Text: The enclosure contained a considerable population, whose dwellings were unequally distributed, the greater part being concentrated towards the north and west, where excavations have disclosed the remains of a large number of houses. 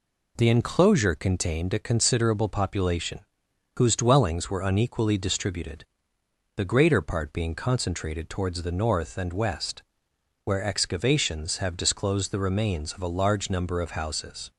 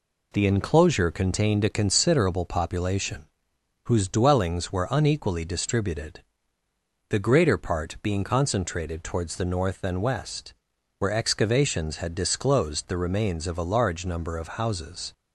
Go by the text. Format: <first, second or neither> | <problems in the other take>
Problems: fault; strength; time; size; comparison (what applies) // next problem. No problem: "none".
first | says "had" for "have"; at 11.9 s